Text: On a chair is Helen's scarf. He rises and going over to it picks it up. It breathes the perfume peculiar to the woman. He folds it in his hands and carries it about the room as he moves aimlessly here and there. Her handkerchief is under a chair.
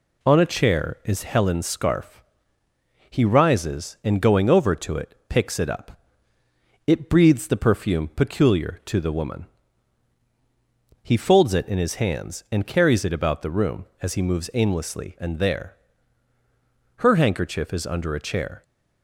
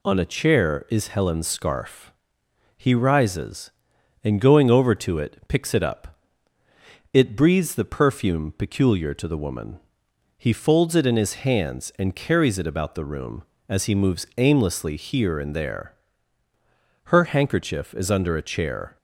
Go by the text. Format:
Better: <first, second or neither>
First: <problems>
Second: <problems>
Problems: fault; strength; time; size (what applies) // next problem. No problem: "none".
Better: second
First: skips "here"; at 15.1 s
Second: none